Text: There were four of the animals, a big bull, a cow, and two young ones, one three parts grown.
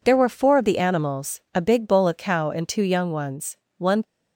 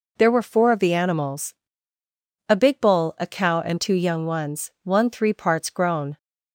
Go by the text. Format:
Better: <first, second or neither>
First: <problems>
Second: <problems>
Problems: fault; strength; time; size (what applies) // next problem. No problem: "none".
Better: second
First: stops before "three parts grown"; at 4.0 s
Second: none